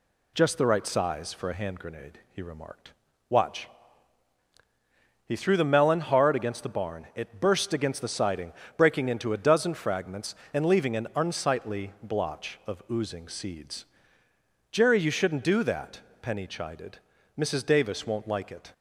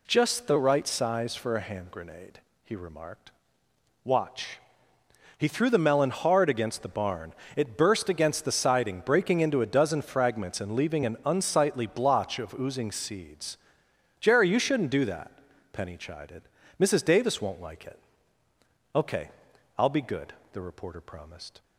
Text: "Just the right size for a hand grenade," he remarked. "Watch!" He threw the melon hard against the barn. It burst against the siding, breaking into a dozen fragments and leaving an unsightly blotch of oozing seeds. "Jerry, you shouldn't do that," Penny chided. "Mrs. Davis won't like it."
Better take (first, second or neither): first